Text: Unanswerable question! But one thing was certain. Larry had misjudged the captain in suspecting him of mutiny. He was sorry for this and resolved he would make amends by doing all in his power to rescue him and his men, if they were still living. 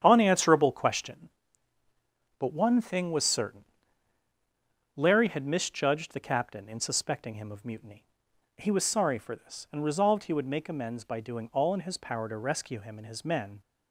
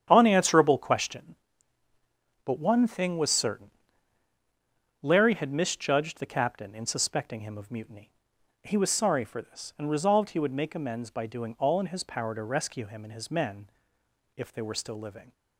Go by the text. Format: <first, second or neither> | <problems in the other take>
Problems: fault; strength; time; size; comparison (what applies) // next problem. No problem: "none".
second | starts louder than the rest; strong; until 1.0 s; 9 dB; strong in the second // stops before "if they were still living"; at 13.6 s